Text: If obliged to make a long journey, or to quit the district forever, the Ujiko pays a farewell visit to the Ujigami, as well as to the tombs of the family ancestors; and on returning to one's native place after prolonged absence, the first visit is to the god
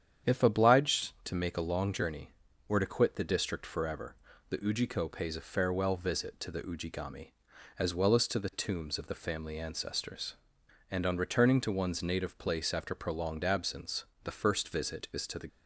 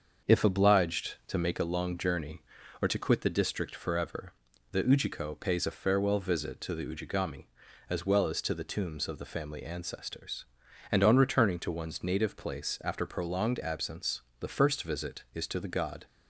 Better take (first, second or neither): second